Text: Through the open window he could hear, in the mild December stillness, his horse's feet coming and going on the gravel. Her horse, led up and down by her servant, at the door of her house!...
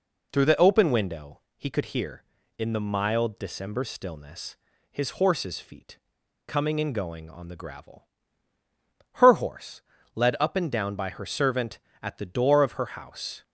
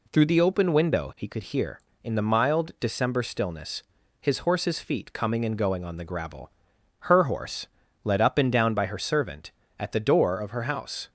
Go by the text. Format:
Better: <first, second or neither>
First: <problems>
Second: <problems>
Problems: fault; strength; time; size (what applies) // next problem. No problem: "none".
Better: second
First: pauses between "window" and "he"; slight; at 1.3 s; 0.16 s long // pauses between "feet" and "coming"; noticeable; at 5.9 s; 0.49 s long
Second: none